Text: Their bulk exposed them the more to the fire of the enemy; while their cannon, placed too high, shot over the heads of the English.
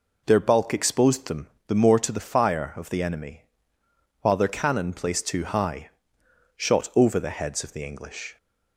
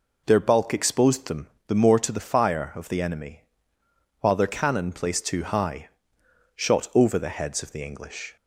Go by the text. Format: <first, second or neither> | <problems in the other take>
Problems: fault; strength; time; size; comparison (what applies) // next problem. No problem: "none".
neither | pauses between "them" and "the"; slight; the same in both